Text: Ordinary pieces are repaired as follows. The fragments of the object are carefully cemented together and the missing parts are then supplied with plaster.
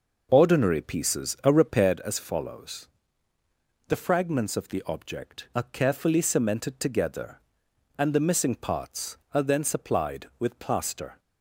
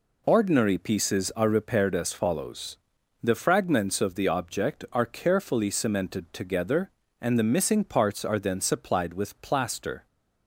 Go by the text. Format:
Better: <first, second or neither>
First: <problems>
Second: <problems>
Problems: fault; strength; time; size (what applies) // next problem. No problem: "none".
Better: second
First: starts louder than the rest; noticeable; until 1.9 s; 5.5 dB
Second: none